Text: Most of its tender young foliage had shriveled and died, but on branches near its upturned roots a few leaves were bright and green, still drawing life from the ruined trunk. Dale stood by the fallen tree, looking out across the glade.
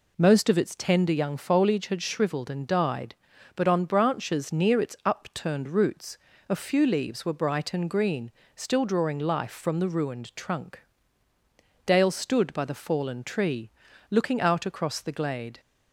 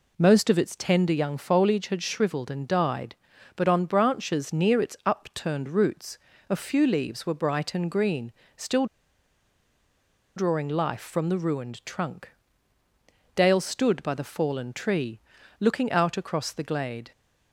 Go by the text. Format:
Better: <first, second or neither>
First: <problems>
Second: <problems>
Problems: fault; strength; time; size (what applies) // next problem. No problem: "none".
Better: first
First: pauses between "roots" and "a"; slight; at 6.1 s; 0.32 s long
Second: pauses between "roots" and "a"; slight; at 6.1 s; 0.32 s long // pauses between "still" and "drawing"; strong; at 8.8 s; 1.5 s long